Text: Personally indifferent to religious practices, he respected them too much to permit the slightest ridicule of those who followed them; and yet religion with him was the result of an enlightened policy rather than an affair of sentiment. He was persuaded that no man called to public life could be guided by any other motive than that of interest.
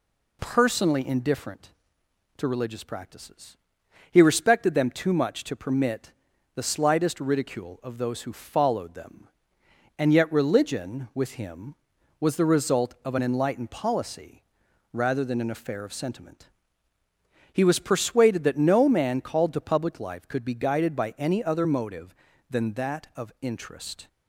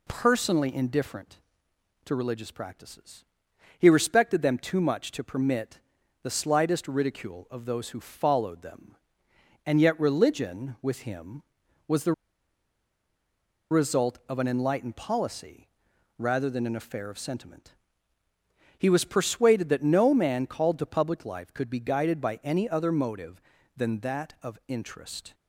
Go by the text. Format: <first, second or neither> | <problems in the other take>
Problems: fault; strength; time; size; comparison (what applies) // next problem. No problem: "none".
first | pauses between "permit" and "the"; at 5.7 s; 0.42 s long; also in the first // pauses between "the" and "result"; strong; at 12.1 s; 1.5 s long // pauses between "policy" and "rather"; noticeable; at 15.6 s; 0.50 s long; noticeable in the first